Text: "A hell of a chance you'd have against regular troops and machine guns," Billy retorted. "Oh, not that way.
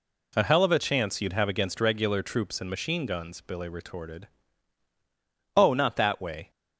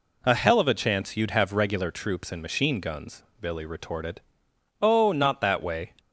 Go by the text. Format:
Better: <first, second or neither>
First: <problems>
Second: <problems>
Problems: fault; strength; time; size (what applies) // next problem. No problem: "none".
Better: first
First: none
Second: skips "against"; at 1.5 s